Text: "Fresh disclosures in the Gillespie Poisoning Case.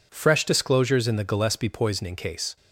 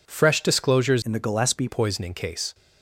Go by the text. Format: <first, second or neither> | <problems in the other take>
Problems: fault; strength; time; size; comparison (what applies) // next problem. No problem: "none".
first | changes voice from "in" to "Gillespie"; from 1.0 to 1.6 s; 0.6 s long